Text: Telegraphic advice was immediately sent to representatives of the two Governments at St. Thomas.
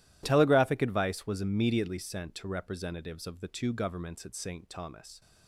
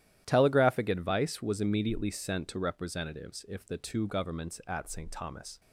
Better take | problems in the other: first | starts louder than the rest; strong; until 1.2 s; 12 dB // says "if" for "of"; at 3.4 s

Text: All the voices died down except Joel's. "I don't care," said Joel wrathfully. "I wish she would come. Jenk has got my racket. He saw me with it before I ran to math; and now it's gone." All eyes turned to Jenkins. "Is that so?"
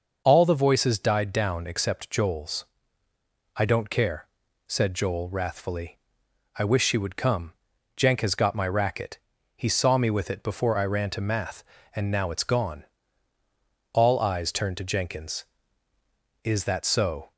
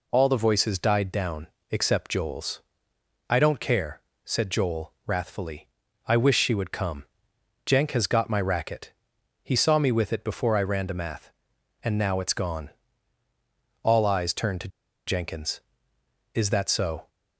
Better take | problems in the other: first | pauses between "down" and "except"; slight; at 1.4 s; 0.24 s long // pauses between "to" and "Jenkins"; at 14.6 s; 0.39 s long

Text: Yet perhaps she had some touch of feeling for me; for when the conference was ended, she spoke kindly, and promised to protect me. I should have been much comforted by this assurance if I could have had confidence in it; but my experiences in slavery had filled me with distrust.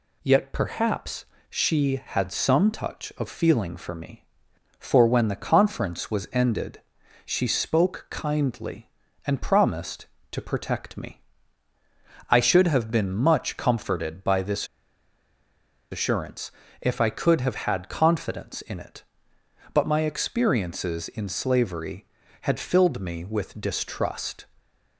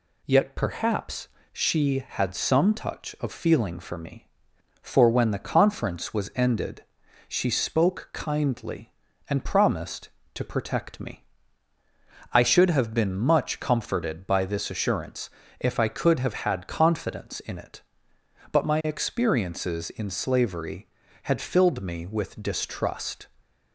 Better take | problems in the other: second | pauses between "perhaps" and "she"; slight; at 1.2 s; 0.24 s long; slight in the second // pauses between "this" and "assurance"; strong; at 14.6 s; 1.2 s long // pauses between "assurance" and "if"; slight; at 16.4 s; 0.30 s long; slight in the second

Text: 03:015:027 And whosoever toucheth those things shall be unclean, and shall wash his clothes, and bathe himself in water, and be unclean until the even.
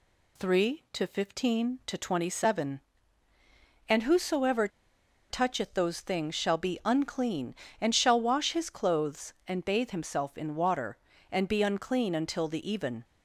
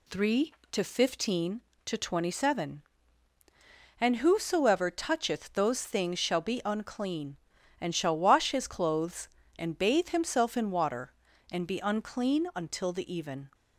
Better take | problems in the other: second | pauses between "whosoever" and "toucheth"; noticeable; at 4.6 s; 0.61 s long

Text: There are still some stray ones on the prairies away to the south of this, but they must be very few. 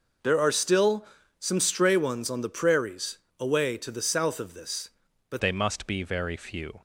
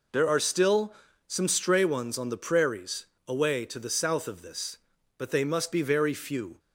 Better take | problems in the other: second | pauses between "still" and "some"; slight; at 1.0 s; 0.34 s long; slight in the second // pauses between "prairies" and "away"; slight; at 3.1 s; 0.22 s long; slight in the second // changes voice at "they"; from 5.3 s on; 1.5 s long

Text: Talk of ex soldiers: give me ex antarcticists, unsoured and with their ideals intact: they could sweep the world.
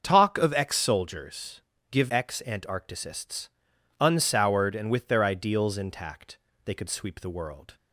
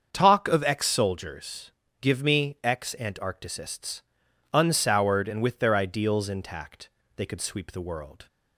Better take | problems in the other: second | starts louder than the rest; until 1.0 s; 6.5 dB; also in the second // skips "me"; at 2.0 s

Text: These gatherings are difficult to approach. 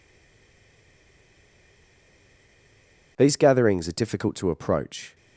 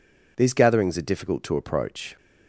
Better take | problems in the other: second | stays silent before the first word; strong; until 3.1 s; 3.1 s long

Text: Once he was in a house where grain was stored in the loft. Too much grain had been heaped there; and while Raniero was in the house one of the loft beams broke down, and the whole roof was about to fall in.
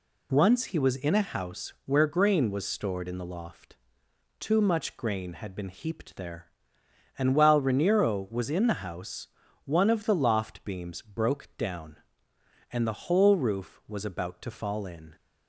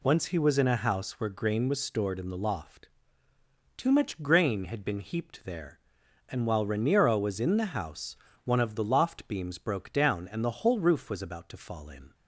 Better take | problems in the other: neither | pauses between "house" and "one"; the same in both

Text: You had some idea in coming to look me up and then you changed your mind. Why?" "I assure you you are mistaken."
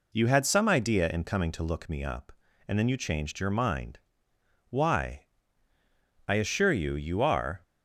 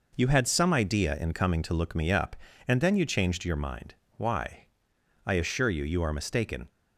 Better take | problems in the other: second | stops before "mistaken"; at 7.6 s

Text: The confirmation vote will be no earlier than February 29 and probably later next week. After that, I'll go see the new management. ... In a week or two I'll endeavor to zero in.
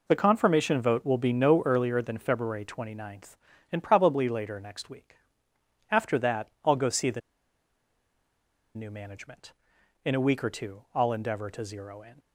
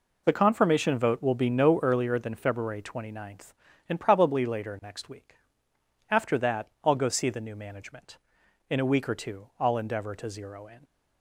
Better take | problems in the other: second | pauses between "the" and "new"; strong; at 7.2 s; 1.5 s long

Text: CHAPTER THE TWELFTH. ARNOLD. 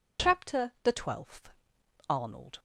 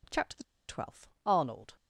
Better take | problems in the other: first | pauses between "THE" and "TWELFTH"; slight; at 0.4 s; 0.25 s long

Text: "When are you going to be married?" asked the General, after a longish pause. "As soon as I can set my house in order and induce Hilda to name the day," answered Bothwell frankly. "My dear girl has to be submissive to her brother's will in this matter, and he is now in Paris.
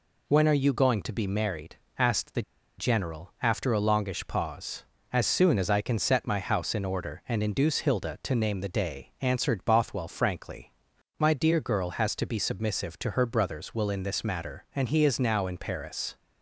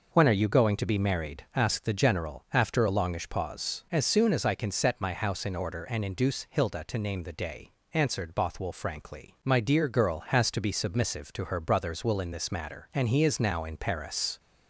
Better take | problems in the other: second | pauses between "the" and "General"; at 2.4 s; 0.36 s long

